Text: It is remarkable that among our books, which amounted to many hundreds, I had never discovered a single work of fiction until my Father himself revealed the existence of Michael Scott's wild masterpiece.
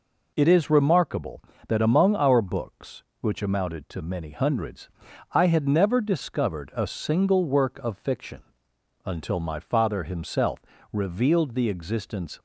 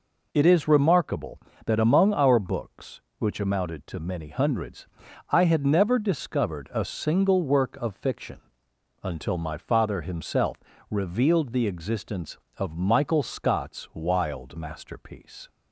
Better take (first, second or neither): second